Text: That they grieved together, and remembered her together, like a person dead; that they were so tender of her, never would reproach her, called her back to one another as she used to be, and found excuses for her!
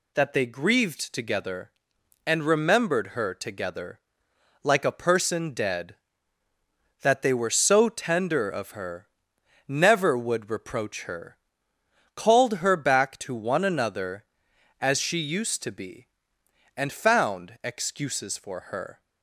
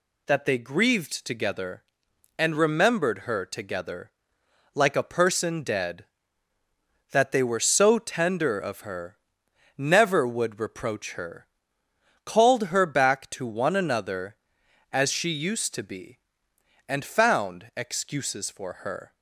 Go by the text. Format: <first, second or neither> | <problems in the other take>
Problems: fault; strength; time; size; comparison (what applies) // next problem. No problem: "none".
neither | none